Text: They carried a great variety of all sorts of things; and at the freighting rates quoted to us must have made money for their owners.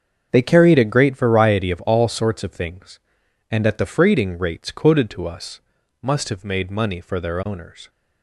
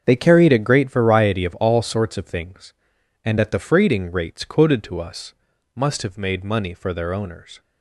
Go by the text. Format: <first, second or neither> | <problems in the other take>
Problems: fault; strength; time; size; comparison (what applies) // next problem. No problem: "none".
neither | starts louder than the rest; the same in both // pauses between "us" and "must"; the same in both